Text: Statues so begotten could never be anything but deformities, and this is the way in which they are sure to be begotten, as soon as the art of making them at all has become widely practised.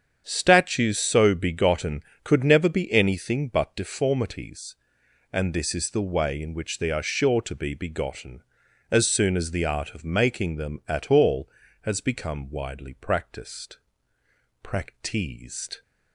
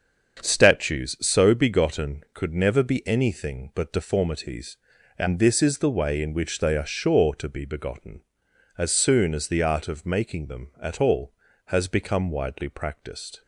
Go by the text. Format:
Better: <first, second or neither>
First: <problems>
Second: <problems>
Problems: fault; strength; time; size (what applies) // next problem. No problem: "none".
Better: second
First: starts louder than the rest; strong; until 1.2 s; 8 dB // says "practised" twice; at 14.6 s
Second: starts louder than the rest; until 1.4 s; 7 dB